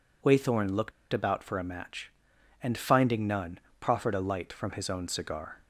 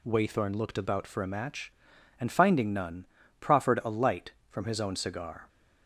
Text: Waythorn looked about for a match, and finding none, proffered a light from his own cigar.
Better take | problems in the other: second | pauses between "looked" and "about"; slight; at 0.9 s; 0.20 s long

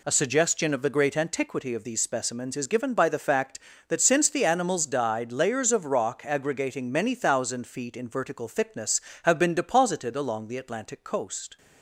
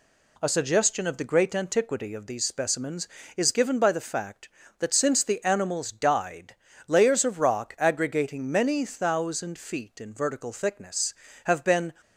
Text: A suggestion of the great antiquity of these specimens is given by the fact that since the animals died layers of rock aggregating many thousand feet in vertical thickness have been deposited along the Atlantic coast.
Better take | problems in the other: first | pauses between "died" and "layers"; slight; at 6.5 s; 0.32 s long // stops before "deposited along the Atlantic coast"; at 12.0 s

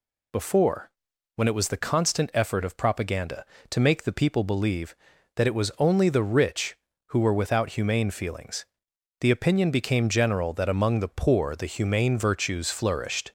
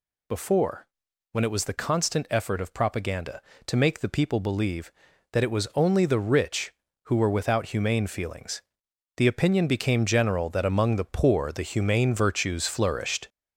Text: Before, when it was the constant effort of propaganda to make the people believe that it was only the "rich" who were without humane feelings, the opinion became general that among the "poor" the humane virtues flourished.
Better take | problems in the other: first | gets louder; noticeable; throughout; 4 dB

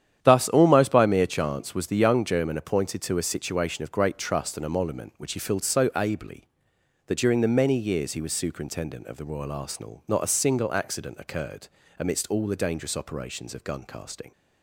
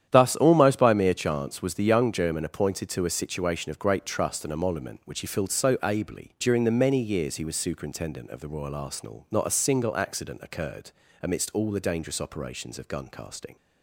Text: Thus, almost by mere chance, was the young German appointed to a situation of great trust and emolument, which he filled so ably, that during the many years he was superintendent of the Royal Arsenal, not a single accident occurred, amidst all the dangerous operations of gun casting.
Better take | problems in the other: first | starts louder than the rest; strong; until 1.1 s; 10 dB; strong in the first // skips "that"; at 6.3 s

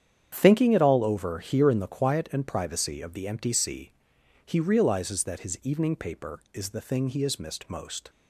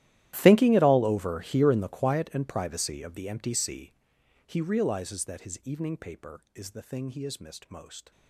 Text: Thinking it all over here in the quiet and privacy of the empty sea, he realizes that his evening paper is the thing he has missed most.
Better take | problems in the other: first | gets quieter; strong; throughout; 21.5 dB // starts louder than the rest; strong; until 1.3 s; 14 dB; strong in the first

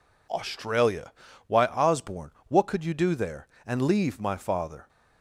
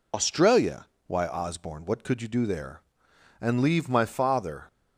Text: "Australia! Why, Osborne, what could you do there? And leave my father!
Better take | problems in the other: first | loses the start of "Australia"; at 0.1 s; 85 ms

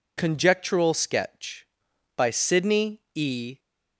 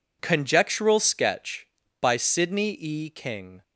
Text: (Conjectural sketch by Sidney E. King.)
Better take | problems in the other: second | pauses between "Sidney" and "E"; slight; at 2.9 s; 0.16 s long // stops before "King"; at 3.5 s

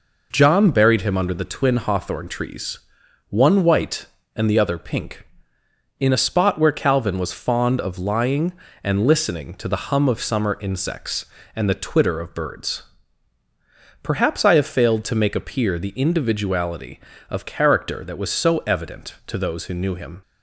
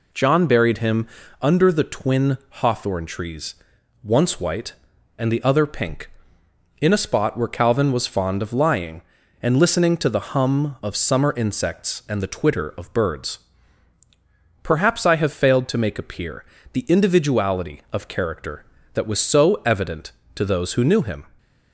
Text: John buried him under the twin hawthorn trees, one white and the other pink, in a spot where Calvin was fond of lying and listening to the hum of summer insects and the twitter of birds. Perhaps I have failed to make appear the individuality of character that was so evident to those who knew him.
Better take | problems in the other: first | pauses between "him" and "under"; slight; at 1.0 s; 0.34 s long // says "once" for "one"; at 4.0 s // pauses between "appear" and "the"; slight; at 16.4 s; 0.30 s long

